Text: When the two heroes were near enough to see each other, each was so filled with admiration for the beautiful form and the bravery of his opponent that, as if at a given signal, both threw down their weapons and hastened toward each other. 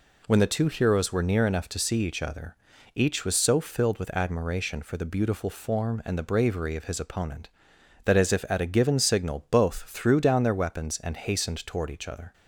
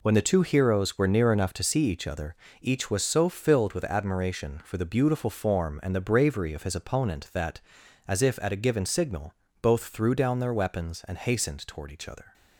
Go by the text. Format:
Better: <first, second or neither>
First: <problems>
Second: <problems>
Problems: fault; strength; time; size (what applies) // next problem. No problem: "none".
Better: neither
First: none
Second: none